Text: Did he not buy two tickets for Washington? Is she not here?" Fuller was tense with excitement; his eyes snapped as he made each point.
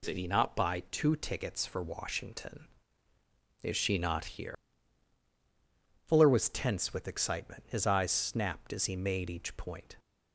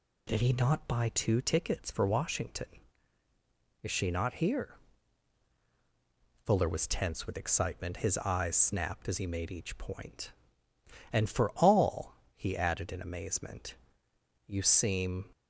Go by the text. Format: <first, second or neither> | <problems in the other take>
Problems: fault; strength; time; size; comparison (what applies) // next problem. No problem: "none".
first | goes on to say "And for all he added in amazement you seem"; strong; from 11.1 s on; 4.1 s long